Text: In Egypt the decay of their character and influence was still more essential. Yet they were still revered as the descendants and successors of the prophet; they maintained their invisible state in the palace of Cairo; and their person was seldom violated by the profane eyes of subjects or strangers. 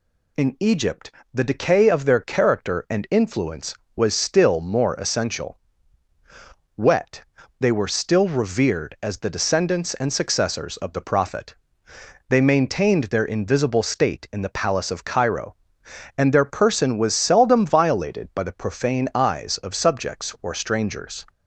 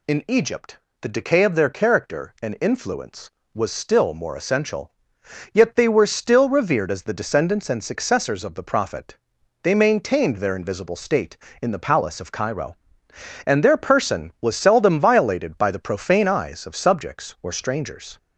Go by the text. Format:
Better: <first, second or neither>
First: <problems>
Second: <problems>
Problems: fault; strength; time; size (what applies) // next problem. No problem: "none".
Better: second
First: pauses between "Egypt" and "the"; slight; at 1.1 s; 0.20 s long // says "Wet" for "Yet"; at 6.7 s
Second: pauses between "Egypt" and "the"; slight; at 0.7 s; 0.20 s long